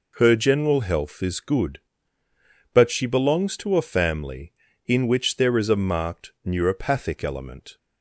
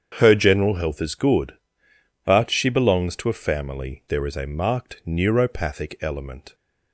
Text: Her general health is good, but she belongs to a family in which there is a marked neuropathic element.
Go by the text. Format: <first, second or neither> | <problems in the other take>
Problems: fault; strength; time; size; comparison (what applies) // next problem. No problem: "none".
first | starts louder than the rest; strong; until 1.1 s; 7.5 dB // skips "in which"; at 4.0 s